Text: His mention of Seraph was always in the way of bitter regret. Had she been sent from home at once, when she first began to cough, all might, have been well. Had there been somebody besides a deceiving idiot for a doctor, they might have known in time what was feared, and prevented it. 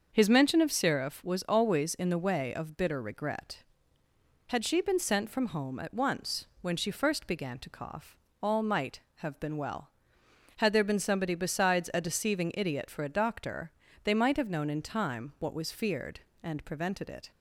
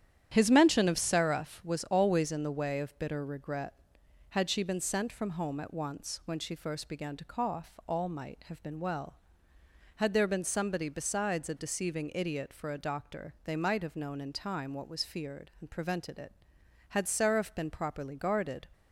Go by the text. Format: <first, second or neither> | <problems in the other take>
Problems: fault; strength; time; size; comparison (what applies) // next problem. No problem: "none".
first | starts louder than the rest; strong; until 1.3 s; 10 dB; also in the first // goes on to say "Had Seraph been properly guarded"; strong; from 16.8 s on; 1.7 s long